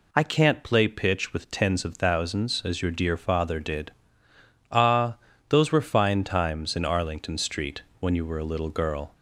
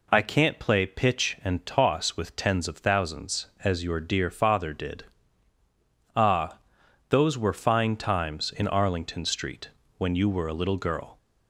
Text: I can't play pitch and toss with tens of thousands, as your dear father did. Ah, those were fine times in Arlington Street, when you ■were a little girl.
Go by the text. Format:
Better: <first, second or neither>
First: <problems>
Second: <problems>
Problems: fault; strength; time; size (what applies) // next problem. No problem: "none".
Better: second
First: skips "and toss"; at 1.3 s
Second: none